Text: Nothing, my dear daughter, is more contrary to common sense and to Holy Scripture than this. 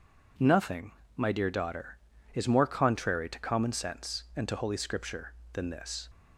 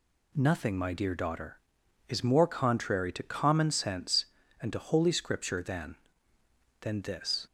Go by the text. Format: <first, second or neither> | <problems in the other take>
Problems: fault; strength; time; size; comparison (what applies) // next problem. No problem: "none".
first | says "than" twice; at 6.7 s